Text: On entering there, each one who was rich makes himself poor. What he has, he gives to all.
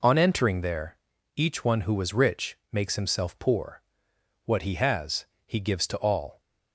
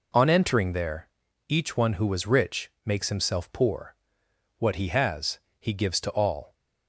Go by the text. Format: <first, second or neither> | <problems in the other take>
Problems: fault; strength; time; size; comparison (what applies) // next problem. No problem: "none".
neither | pauses between "rich" and "makes"; slight; the same in both